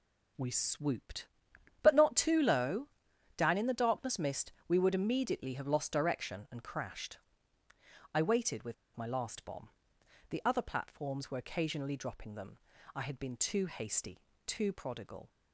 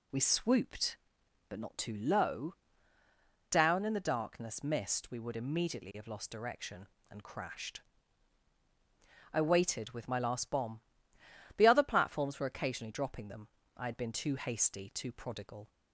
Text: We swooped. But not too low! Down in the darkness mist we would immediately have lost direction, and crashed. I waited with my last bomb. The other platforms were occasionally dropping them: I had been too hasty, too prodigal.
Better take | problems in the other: second | pauses between "mist" and "we"; slight; at 4.5 s; 0.16 s long // pauses between "with" and "my"; slight; at 8.7 s; 0.21 s long

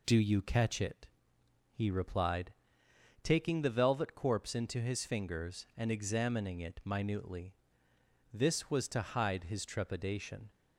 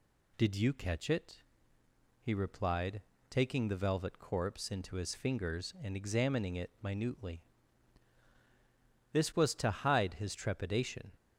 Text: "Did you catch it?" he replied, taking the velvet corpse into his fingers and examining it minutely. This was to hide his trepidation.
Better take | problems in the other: second | says "Do" for "Did"; at 0.0 s

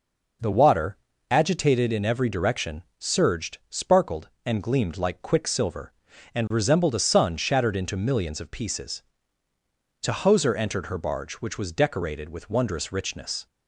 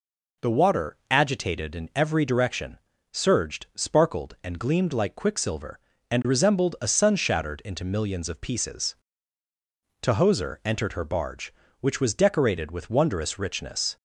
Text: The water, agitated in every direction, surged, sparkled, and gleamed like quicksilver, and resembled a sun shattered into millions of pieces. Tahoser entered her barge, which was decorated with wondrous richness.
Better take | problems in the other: neither | none

